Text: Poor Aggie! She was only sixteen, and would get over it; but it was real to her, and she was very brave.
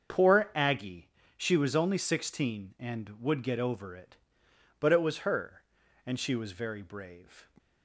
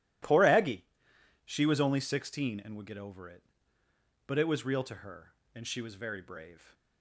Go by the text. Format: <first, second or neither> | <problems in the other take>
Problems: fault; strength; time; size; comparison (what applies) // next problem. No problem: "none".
second | starts louder than the rest; until 1.4 s; 7 dB // skips "real to"; at 5.1 s